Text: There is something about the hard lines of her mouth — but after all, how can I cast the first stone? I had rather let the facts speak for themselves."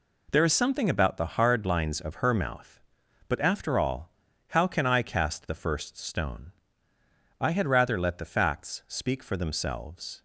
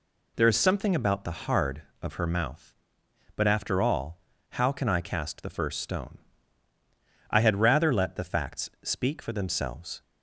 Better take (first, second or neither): first